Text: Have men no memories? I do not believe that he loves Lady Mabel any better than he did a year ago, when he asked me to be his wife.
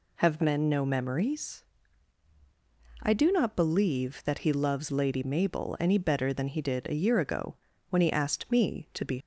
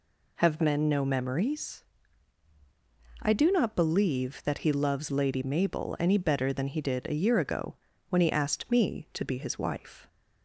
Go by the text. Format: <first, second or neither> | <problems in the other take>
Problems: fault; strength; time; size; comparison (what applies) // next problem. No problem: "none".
second | stops before "his wife"; at 9.1 s